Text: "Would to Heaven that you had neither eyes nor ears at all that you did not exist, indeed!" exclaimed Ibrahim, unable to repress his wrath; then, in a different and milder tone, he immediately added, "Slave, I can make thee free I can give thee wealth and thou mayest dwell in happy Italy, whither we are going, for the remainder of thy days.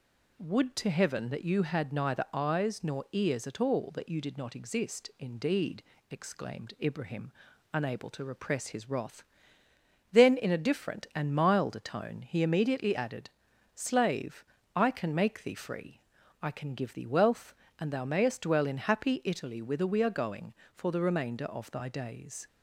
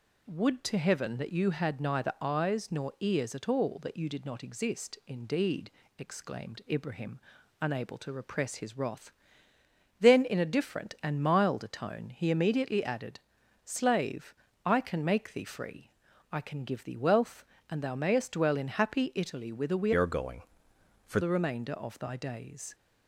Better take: first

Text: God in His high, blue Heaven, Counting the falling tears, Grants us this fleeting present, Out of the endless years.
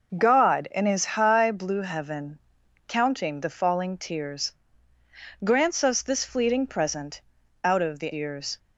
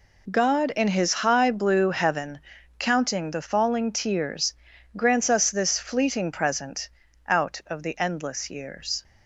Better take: second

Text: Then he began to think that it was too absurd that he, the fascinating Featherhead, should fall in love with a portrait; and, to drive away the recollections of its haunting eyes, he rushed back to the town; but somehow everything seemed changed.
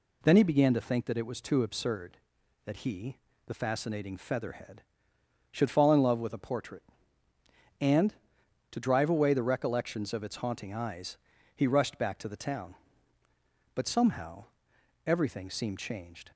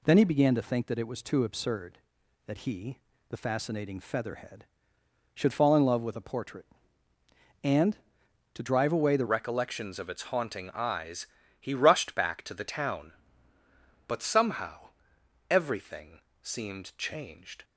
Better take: first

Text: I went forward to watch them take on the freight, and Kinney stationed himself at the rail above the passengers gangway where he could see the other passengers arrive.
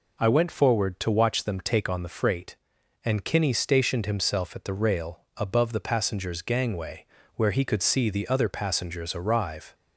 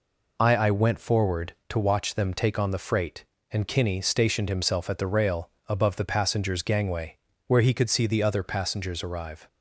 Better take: first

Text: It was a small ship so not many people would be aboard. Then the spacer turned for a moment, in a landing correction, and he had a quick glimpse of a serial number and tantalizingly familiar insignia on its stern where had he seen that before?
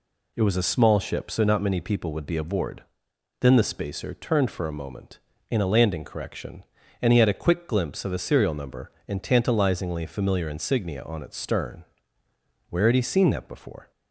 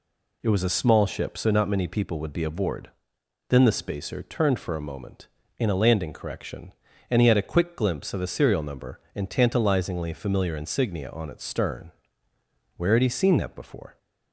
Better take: neither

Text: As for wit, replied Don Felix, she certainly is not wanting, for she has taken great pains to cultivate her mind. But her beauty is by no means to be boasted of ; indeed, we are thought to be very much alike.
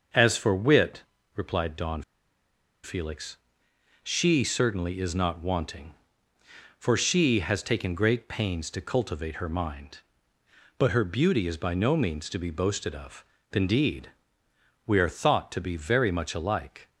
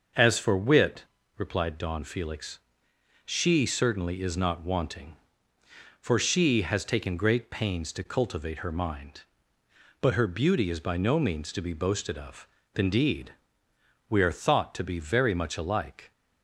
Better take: second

